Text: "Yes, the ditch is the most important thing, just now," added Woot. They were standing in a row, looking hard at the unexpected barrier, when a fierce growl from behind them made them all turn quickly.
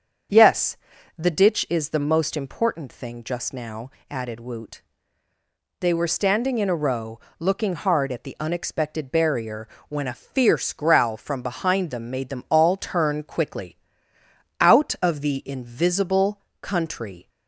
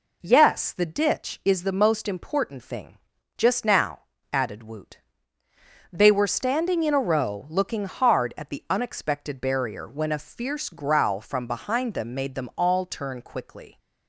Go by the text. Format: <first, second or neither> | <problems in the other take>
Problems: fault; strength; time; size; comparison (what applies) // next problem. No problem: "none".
second | starts louder than the rest; strong; until 1.7 s; 7.5 dB // goes on to say "Out of the invisible country"; strong; from 14.6 s on; 2.6 s long